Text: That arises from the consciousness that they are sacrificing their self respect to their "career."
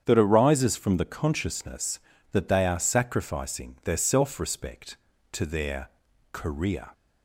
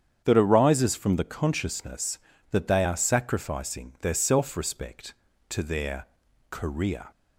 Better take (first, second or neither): neither